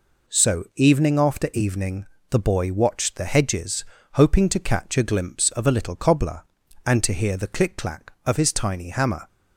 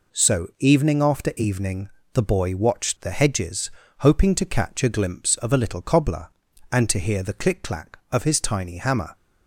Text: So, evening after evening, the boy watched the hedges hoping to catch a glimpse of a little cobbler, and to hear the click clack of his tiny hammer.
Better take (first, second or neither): neither